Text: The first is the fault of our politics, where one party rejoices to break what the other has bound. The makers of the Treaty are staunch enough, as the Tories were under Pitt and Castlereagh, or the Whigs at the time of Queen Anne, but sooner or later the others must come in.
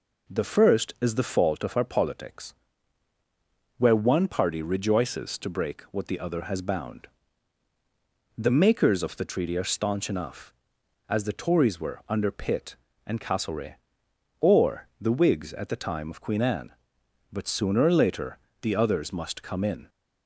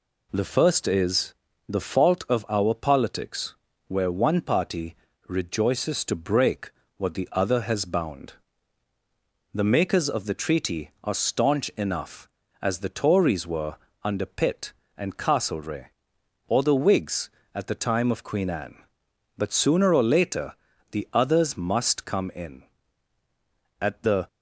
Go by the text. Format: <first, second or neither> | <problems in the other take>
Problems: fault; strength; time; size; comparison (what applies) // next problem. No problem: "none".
first | pauses between "is" and "the"; slight; at 1.3 s; 0.36 s long // pauses between "party" and "rejoices"; slight; at 4.9 s; 0.34 s long // pauses between "break" and "what"; slight; at 6.7 s; 0.26 s long // pauses between "were" and "under"; slight; at 13.7 s; 0.26 s long // pauses between "later" and "the"; slight; at 20.5 s; 0.36 s long; slight in the first // goes on to say "At the"; slight; from 23.8 s on; 0.46 s long